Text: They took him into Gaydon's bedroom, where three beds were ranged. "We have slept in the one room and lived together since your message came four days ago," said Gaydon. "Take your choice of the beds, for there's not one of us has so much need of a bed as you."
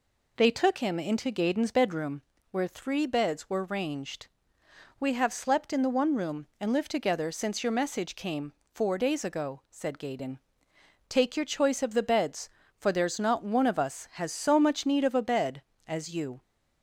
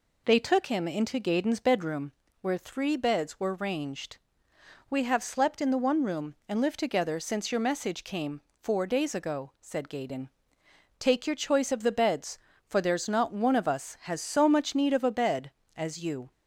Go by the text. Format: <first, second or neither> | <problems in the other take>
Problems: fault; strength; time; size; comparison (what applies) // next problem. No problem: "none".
neither | pauses between "came" and "four"; slight; the same in both